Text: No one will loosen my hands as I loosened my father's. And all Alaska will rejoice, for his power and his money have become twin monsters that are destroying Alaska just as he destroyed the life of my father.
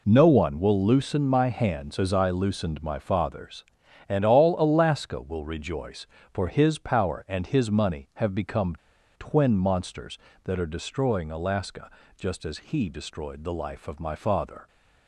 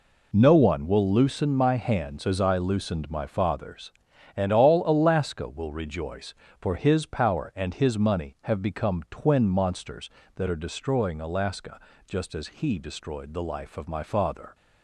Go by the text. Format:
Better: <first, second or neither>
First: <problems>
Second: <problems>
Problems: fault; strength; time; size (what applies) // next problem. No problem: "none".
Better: second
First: pauses between "become" and "twin"; at 8.7 s; 0.42 s long // pauses between "Alaska" and "just"; slight; at 11.9 s; 0.26 s long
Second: pauses between "Alaska" and "just"; slight; at 11.8 s; 0.26 s long